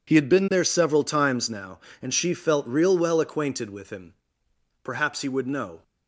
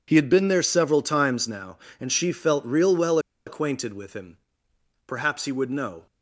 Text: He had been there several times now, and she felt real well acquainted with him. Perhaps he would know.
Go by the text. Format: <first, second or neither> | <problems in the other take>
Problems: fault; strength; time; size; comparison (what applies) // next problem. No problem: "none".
first | pauses between "well" and "acquainted"; slight; at 3.1 s; 0.27 s long